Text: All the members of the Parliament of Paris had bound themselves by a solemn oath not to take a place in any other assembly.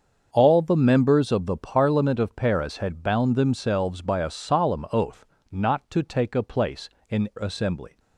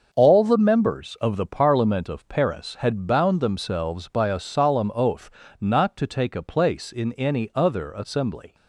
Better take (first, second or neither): second